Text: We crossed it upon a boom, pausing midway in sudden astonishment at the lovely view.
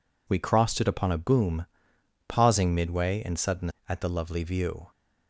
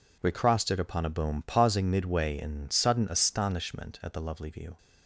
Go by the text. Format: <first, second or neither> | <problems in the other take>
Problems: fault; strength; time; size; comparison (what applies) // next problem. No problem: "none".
second | skips "astonishment"; at 3.7 s